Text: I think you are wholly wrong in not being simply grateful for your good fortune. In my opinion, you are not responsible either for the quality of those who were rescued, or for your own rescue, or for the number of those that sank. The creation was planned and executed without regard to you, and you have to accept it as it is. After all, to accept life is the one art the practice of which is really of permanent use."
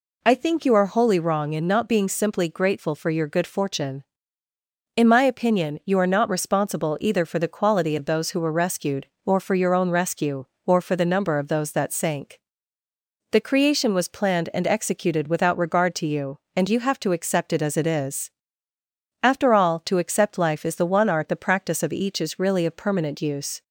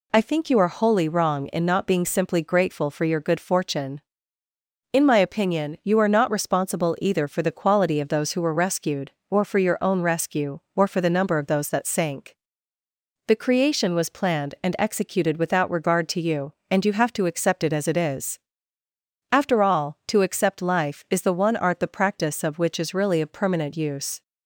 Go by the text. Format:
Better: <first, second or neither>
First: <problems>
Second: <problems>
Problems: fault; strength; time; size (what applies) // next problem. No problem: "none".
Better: second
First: says "each" for "which"; at 21.9 s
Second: none